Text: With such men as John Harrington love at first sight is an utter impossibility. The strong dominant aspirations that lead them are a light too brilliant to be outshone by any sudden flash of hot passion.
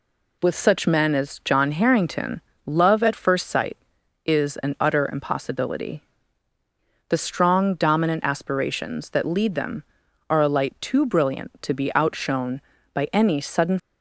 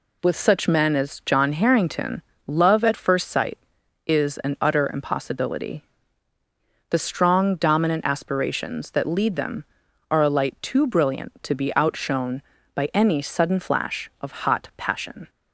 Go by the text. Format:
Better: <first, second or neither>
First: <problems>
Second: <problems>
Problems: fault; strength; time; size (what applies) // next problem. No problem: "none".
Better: second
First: pauses between "Harrington" and "love"; slight; at 2.4 s; 0.24 s long // stops before "flash of hot passion"; at 13.7 s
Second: pauses between "Harrington" and "love"; slight; at 2.2 s; 0.24 s long